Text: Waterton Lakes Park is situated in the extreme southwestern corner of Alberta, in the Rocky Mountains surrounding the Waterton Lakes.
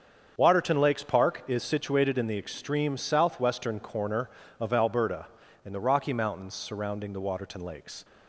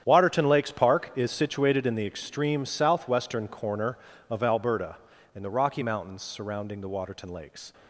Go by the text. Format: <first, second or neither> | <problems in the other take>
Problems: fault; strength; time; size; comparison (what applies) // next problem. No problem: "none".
first | gets quieter; strong; throughout; 13 dB // starts louder than the rest; strong; until 1.0 s; 9 dB; also in the first